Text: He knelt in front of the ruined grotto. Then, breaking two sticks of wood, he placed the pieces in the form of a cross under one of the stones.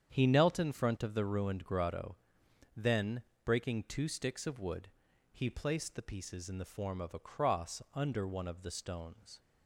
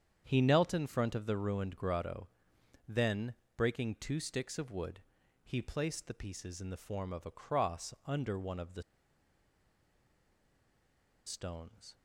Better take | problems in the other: first | starts louder than the rest; strong; until 1.2 s; 8 dB; strong in the first // pauses between "the" and "stones"; strong; at 8.8 s; 2.4 s long

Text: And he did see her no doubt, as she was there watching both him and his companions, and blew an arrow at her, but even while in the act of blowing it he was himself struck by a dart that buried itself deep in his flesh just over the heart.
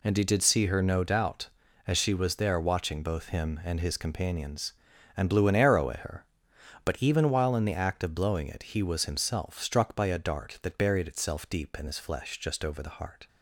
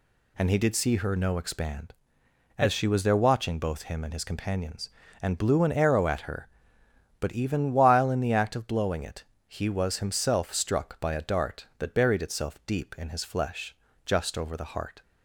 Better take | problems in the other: first | says "expand" for "doubt"; at 1.3 s // pauses between "it" and "he"; slight; at 9.2 s; 0.24 s long // pauses between "flesh" and "just"; slight; at 13.7 s; 0.28 s long

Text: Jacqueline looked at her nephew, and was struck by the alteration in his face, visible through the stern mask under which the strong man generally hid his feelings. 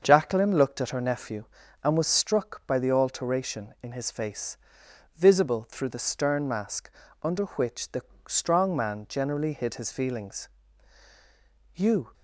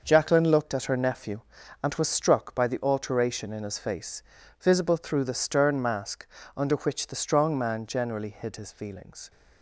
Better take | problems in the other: second | starts louder than the rest; until 1.0 s; 6.5 dB // pauses between "mask" and "under"; slight; at 6.8 s; 0.34 s long; slight in the second // pauses between "the" and "strong"; slight; at 8.0 s; 0.26 s long // goes on to say "You"; slight; from 11.7 s on; 0.38 s long

